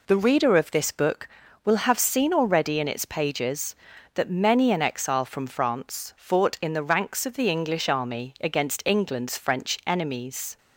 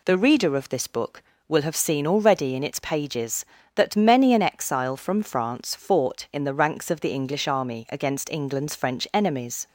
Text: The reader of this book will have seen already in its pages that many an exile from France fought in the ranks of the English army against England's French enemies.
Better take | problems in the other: neither | none

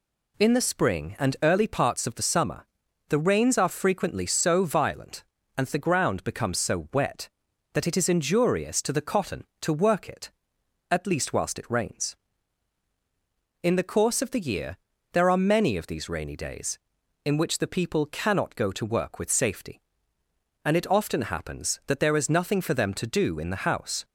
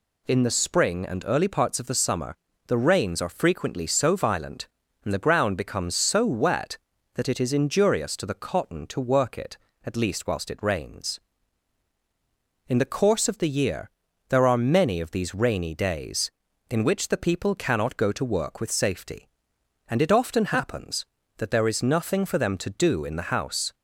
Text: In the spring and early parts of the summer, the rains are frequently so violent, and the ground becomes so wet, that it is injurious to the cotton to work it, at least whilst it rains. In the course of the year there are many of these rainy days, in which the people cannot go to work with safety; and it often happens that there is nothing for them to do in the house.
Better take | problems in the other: neither | pauses between "year" and "there"; the same in both

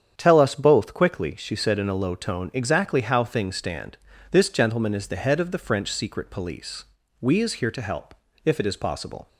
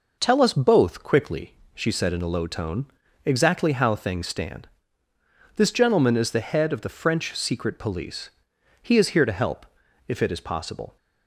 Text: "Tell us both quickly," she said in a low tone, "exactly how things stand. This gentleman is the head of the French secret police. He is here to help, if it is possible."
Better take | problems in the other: second | starts louder than the rest; strong; until 1.1 s; 8.5 dB // says "We" for "He"; at 7.1 s

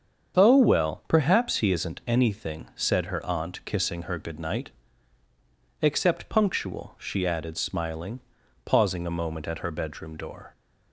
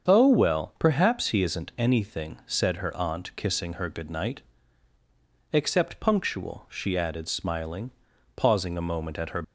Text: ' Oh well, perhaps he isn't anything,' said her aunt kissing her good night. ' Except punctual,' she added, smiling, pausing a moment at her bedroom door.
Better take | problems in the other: first | starts louder than the rest; strong; until 1.1 s; 7.5 dB; strong in the first // stops before "bedroom door"; at 9.4 s

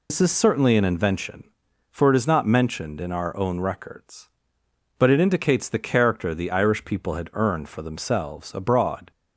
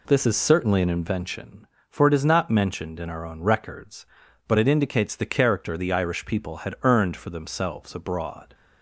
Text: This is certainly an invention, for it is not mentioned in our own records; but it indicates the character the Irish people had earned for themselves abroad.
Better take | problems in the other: second | loses the start of "This"; at 0.0 s; 105 ms

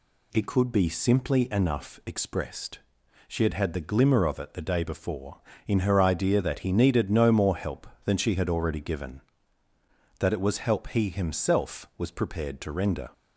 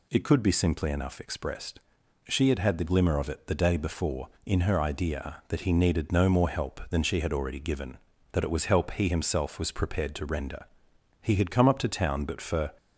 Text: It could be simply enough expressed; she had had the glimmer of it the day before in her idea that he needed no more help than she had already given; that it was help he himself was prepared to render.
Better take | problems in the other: first | goes on to say "He had come up to town but for"; from 11.2 s on; 1.5 s long

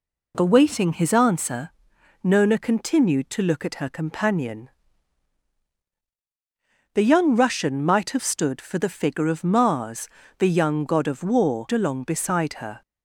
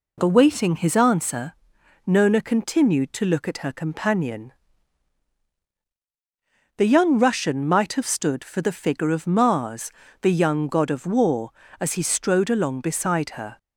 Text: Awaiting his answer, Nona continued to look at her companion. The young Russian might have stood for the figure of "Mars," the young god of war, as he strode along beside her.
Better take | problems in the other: second | skips "as he strode"; at 11.6 s

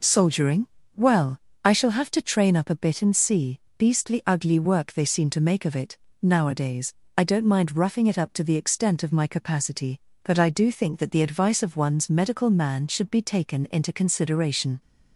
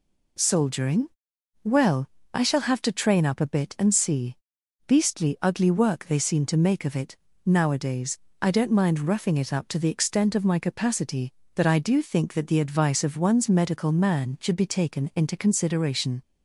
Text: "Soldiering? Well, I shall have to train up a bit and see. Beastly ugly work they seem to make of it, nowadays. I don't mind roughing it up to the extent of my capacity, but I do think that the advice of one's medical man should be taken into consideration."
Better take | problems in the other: neither | none

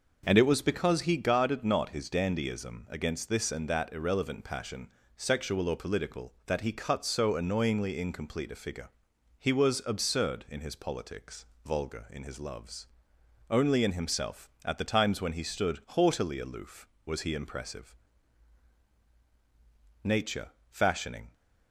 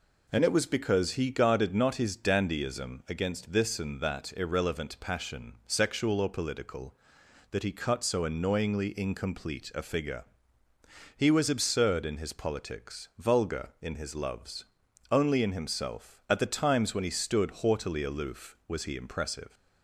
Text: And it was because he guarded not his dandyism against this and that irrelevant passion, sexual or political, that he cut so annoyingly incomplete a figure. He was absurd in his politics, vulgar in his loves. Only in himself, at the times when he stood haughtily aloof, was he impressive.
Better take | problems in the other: second | goes on to say "Nature fashioning"; noticeable; from 20.0 s on; 1.3 s long

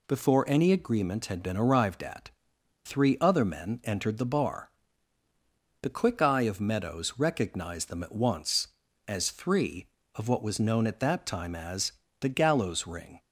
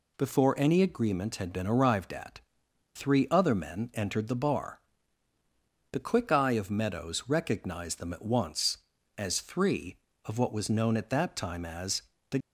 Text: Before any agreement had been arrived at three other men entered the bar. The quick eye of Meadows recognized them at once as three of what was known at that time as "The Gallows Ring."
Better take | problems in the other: first | pauses between "at" and "three"; noticeable; at 2.4 s; 0.54 s long; noticeable in the first // pauses between "as" and "The"; slight; at 12.0 s; 0.28 s long; slight in the first // stops before "Gallows Ring"; at 12.4 s

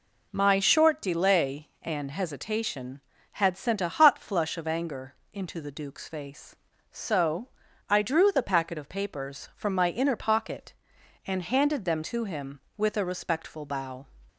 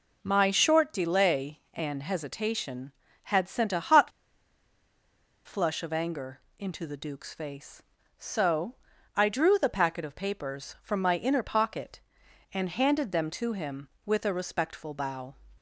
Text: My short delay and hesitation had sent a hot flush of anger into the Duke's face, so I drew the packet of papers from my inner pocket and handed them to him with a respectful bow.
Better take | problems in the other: first | pauses between "hot" and "flush"; strong; at 4.1 s; 1.3 s long // pauses between "anger" and "into"; slight; at 6.4 s; 0.18 s long; slight in the first // pauses between "so" and "I"; at 8.7 s; 0.40 s long; also in the first

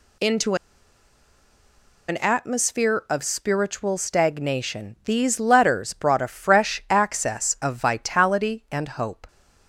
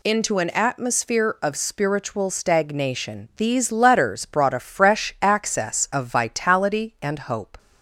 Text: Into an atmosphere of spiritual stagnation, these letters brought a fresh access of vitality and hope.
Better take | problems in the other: second | pauses between "Into" and "an"; strong; at 0.5 s; 1.5 s long

